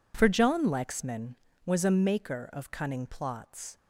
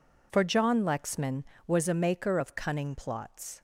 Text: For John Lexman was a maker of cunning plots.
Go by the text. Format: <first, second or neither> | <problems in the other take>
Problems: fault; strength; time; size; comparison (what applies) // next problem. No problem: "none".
neither | none